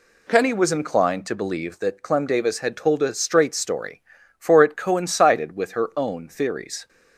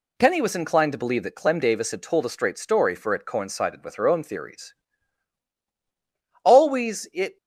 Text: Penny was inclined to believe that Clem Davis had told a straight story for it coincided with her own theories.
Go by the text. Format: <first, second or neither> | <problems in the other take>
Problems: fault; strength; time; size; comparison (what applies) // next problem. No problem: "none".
first | goes on to say "Always it"; noticeable; from 6.4 s on; 0.94 s long